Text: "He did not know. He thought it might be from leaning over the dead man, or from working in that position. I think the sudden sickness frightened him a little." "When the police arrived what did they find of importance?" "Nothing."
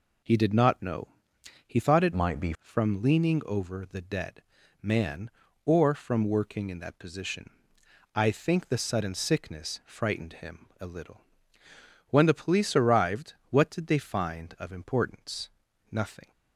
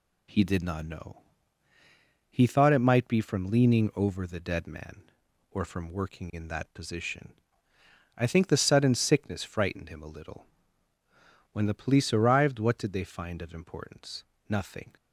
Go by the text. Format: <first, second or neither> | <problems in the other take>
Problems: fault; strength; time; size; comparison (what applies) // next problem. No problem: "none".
second | changes voice from "might" to "be"; from 2.1 to 2.5 s; 0.4 s long // pauses between "dead" and "man"; at 4.4 s; 0.40 s long // pauses between "him" and "a"; slight; at 10.6 s; 0.16 s long // pauses between "arrived" and "what"; slight; at 13.3 s; 0.16 s long